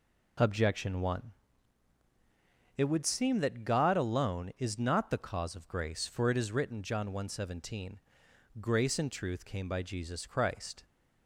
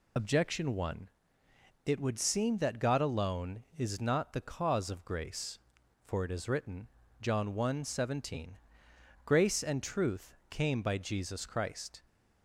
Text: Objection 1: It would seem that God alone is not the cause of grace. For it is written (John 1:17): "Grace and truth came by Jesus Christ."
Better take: first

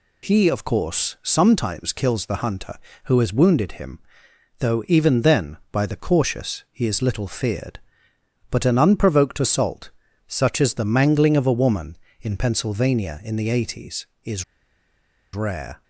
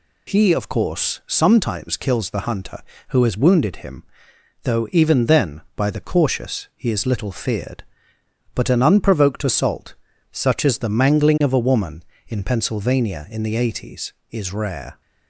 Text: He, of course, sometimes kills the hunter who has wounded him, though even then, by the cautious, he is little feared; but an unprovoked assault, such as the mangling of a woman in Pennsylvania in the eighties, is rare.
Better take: second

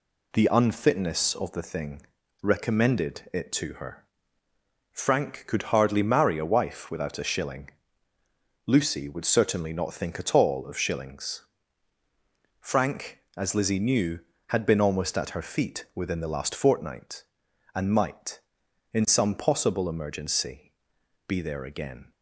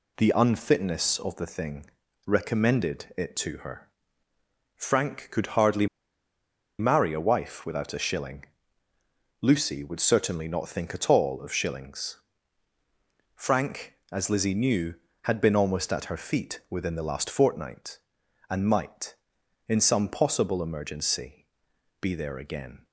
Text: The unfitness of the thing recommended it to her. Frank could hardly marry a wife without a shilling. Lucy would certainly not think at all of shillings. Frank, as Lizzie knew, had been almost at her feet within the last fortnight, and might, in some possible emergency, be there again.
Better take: first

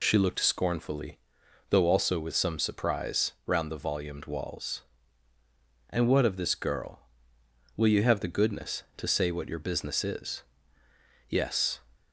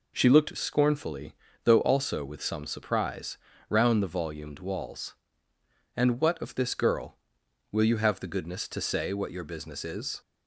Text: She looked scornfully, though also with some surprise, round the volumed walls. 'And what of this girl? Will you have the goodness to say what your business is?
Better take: second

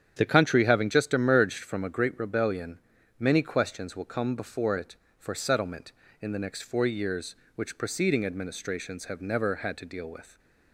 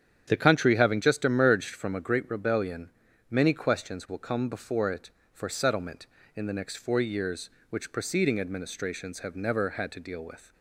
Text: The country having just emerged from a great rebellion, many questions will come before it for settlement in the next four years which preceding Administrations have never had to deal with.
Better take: neither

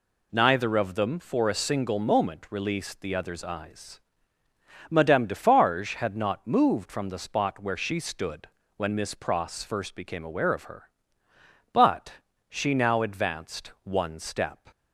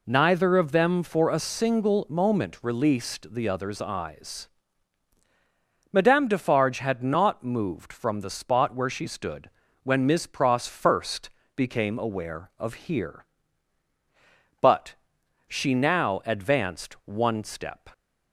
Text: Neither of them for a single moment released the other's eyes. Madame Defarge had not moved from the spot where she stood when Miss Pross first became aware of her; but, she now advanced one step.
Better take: first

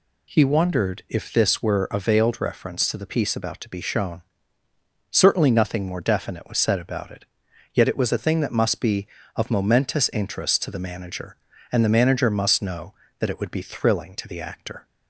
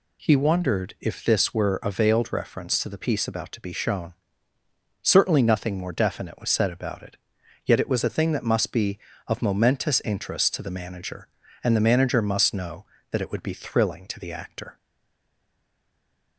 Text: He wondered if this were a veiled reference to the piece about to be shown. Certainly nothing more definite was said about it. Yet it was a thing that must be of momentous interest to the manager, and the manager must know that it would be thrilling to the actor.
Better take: first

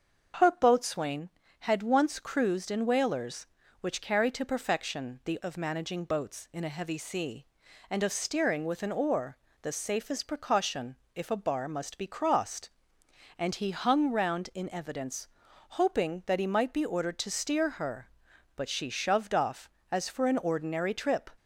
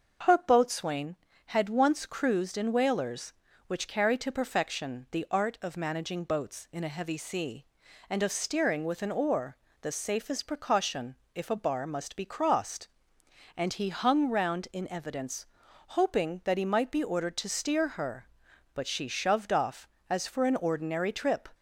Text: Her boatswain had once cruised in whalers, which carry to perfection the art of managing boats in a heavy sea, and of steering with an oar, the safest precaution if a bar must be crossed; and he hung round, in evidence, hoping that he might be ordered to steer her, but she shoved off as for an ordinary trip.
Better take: second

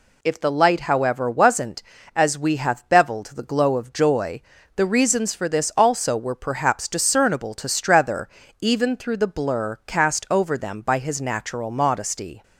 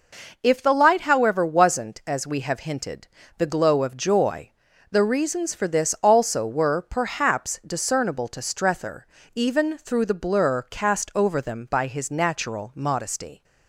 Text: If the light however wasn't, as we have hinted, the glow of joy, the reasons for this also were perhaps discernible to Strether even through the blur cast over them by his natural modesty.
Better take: second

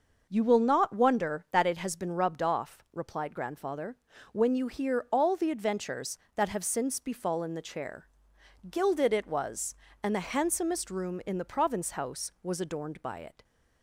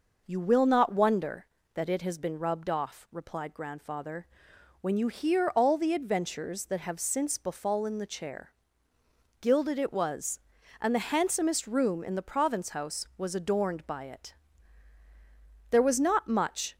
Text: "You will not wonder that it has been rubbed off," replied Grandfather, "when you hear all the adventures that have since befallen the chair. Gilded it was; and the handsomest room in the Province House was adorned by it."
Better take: first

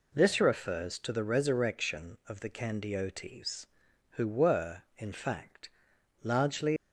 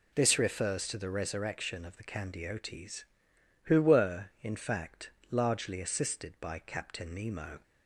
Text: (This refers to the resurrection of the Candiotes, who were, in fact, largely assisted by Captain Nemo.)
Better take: second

